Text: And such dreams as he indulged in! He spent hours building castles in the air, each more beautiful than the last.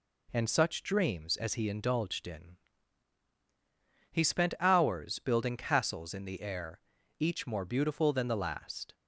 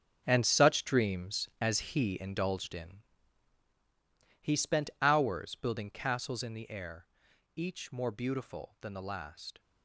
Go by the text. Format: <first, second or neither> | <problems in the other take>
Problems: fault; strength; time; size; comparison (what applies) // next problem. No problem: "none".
first | gets quieter; strong; throughout; 12.5 dB